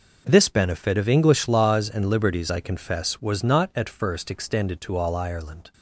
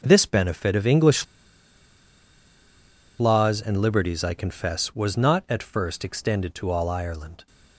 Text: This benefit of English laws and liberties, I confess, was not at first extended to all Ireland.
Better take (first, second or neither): first